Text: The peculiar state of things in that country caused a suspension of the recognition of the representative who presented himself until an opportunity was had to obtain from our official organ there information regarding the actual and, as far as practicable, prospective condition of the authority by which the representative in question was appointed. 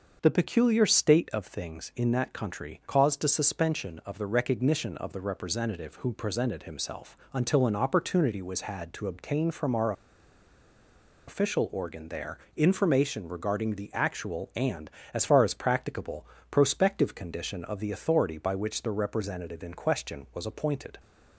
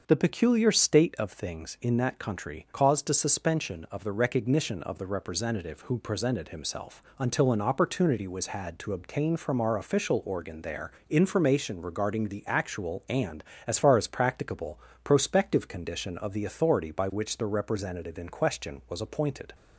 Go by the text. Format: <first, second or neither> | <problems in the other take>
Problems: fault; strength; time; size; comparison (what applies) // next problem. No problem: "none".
second | starts louder than the rest; until 1.2 s; 6 dB; also in the second // pauses between "himself" and "until"; slight; at 7.1 s; 0.16 s long; slight in the second // pauses between "our" and "official"; strong; at 9.9 s; 1.3 s long // pauses between "there" and "information"; slight; at 12.3 s; 0.18 s long; slight in the second